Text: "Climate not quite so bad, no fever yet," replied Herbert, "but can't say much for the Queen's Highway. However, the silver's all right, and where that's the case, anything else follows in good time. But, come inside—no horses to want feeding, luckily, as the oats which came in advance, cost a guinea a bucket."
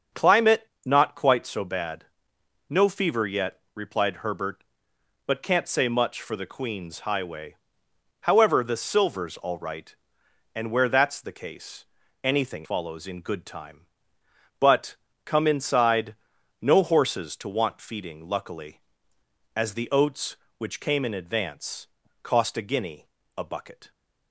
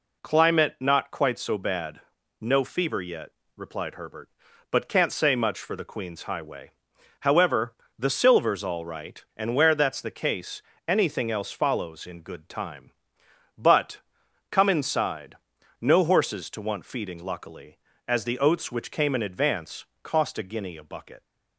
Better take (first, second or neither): second